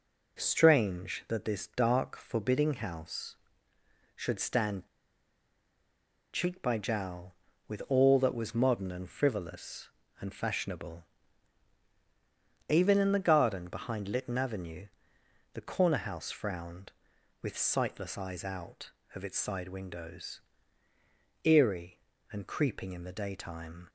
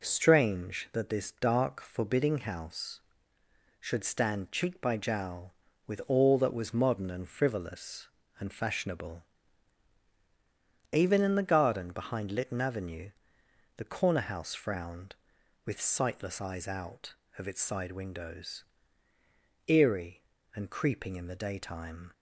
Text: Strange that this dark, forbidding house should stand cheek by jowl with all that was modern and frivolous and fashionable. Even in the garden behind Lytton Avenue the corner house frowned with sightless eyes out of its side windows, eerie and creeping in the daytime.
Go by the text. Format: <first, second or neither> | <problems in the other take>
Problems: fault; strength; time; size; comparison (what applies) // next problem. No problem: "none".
second | pauses between "stand" and "cheek"; strong; at 4.8 s; 1.4 s long // pauses between "Avenue" and "the"; noticeable; at 14.8 s; 0.68 s long; noticeable in the second